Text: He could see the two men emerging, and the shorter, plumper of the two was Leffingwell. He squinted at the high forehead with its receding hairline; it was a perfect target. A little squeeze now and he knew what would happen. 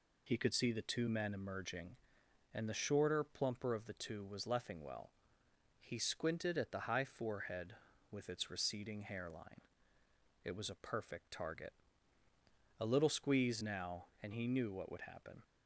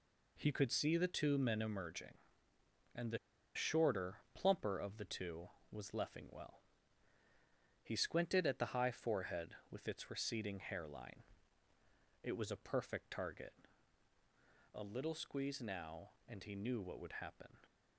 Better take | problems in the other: first | pauses between "the" and "shorter"; at 3.1 s; 0.38 s long

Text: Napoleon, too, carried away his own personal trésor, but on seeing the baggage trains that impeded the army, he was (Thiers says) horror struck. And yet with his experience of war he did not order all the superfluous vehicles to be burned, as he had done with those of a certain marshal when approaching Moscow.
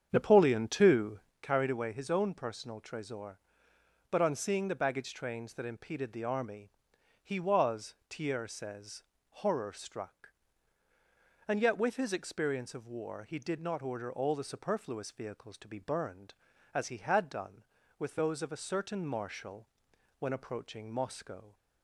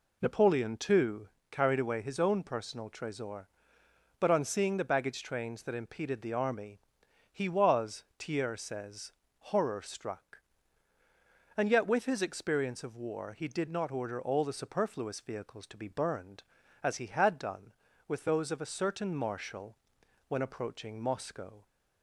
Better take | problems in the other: second | starts louder than the rest; strong; until 1.6 s; 8 dB // pauses between "marshal" and "when"; noticeable; at 19.6 s; 0.50 s long; noticeable in the second

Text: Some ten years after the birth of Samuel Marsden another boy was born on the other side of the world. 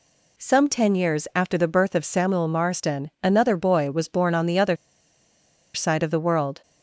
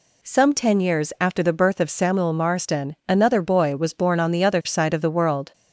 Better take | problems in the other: second | pauses between "other" and "side"; at 4.7 s; 0.98 s long

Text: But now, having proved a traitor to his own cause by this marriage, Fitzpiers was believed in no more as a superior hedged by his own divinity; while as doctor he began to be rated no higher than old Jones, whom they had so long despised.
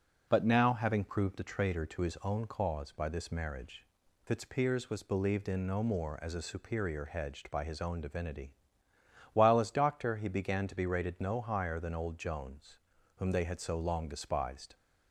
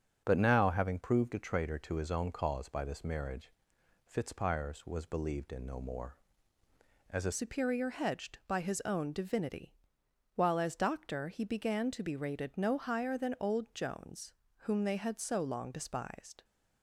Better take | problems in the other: first | starts louder than the rest; strong; until 1.2 s; 7 dB // changes voice at "superior"; from 7.3 s on; 9.1 s long

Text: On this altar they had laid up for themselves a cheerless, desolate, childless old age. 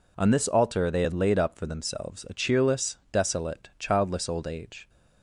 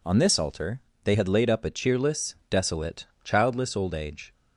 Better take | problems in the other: first | pauses between "altar" and "they"; slight; at 0.8 s; 0.24 s long // skips "for themselves"; at 1.6 s

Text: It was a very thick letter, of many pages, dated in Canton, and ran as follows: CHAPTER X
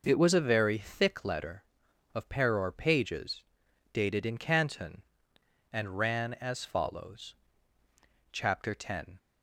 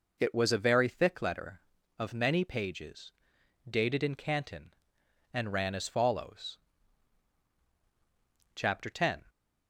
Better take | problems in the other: second | says "peror" for "many"; at 2.2 s

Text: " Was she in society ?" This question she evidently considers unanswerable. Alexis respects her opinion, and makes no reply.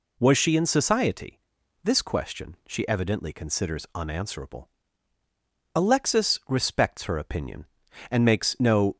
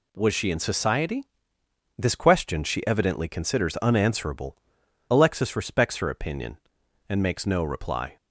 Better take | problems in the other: second | stops before "reply"; at 8.9 s

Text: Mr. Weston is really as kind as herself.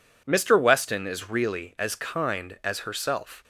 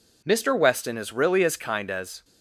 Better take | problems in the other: first | stops before "herself"; at 2.2 s

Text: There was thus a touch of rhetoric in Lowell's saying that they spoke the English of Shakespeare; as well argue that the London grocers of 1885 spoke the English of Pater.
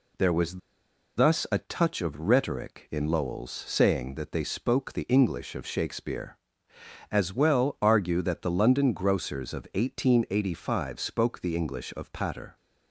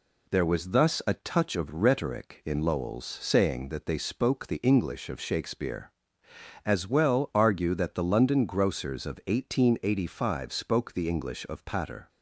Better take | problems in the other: second | pauses between "was" and "thus"; noticeable; at 0.5 s; 0.58 s long

